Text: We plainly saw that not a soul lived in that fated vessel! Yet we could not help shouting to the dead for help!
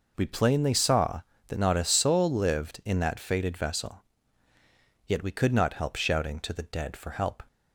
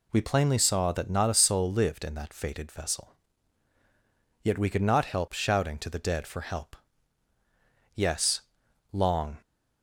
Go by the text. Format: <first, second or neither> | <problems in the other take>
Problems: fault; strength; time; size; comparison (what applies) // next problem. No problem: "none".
first | goes on to say "Yes long"; from 7.9 s on; 1.4 s long